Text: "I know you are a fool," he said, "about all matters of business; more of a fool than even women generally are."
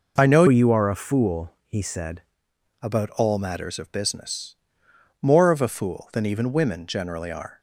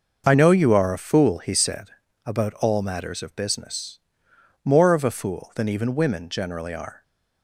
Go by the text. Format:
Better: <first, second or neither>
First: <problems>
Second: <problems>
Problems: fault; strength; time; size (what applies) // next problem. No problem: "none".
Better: second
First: changes voice from "you" to "said"; from 0.4 to 2.2 s; 1.8 s long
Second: none